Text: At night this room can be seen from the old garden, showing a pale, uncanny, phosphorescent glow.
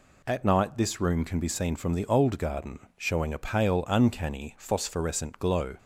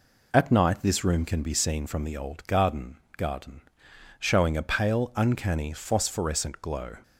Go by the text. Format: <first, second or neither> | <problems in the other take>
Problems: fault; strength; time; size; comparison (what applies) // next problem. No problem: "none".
first | says "garden" twice; at 3.1 s